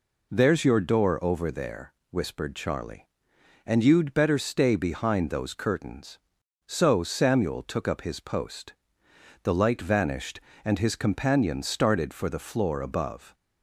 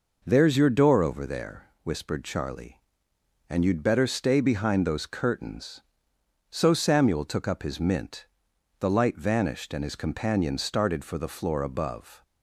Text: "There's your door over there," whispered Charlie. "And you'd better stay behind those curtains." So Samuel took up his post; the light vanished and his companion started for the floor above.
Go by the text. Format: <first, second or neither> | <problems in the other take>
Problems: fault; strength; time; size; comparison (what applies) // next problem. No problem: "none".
first | says "mint" for "post"; at 7.8 s